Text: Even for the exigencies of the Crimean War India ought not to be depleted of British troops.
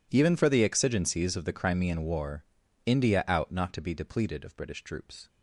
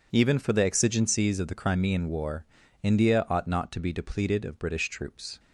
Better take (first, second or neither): second